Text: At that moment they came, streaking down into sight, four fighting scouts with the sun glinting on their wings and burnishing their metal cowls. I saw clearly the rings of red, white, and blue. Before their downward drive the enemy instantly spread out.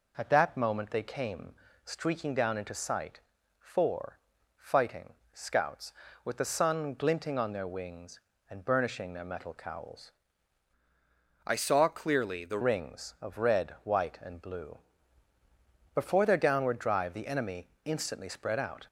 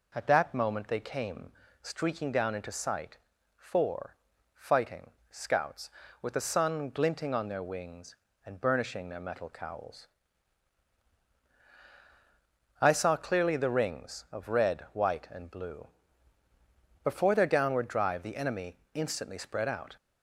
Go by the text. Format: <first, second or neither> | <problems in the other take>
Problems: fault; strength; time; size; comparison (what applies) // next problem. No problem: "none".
second | pauses between "four" and "fighting"; at 4.1 s; 0.40 s long; also in the second // pauses between "fighting" and "scouts"; slight; at 5.1 s; 0.22 s long; slight in the second // changes voice from "I" to "the"; from 11.4 to 12.5 s; 1.1 s long // pauses between "enemy" and "instantly"; slight; at 17.6 s; 0.16 s long; slight in the second